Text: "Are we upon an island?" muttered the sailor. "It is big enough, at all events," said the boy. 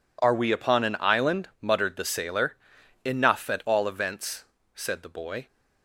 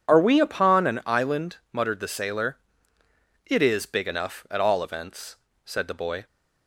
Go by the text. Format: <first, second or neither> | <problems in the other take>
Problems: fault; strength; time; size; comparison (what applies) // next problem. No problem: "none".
second | skips "It is big"; at 2.8 s